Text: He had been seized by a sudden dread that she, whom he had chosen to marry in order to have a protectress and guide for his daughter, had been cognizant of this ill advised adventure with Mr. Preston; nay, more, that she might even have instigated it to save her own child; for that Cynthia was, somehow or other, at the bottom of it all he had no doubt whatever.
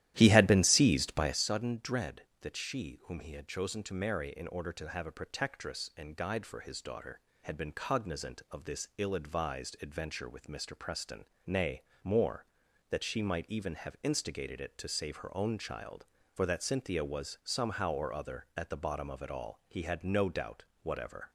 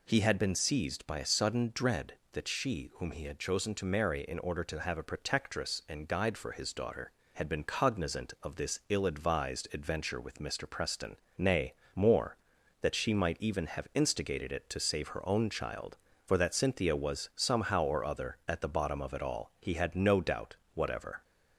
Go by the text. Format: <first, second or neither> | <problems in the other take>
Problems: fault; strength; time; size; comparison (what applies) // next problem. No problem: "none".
second | starts louder than the rest; strong; until 1.4 s; 13 dB // pauses between "doubt" and "whatever"; slight; at 20.6 s; 0.22 s long; slight in the second